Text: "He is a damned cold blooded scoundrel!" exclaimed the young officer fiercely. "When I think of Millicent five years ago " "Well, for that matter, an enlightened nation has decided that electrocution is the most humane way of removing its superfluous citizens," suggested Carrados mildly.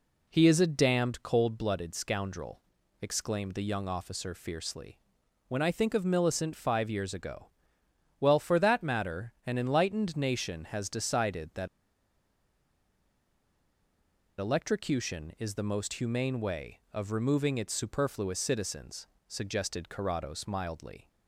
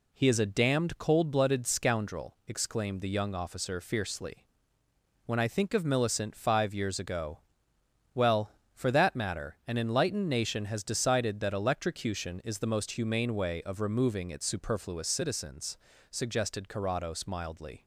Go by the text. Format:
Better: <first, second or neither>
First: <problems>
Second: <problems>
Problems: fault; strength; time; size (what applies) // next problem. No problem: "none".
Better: second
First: pauses between "that" and "electrocution"; strong; at 11.6 s; 2.7 s long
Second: none